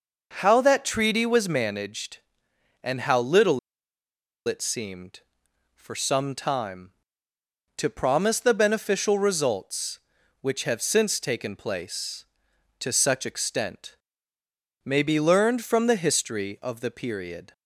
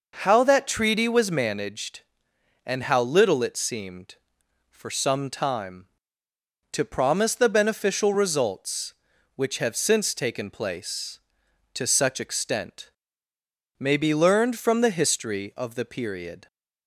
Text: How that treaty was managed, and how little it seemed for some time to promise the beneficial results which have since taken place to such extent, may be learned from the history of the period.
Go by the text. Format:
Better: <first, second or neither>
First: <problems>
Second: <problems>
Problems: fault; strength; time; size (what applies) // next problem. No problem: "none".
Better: second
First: pauses between "little" and "it"; noticeable; at 3.5 s; 0.89 s long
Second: none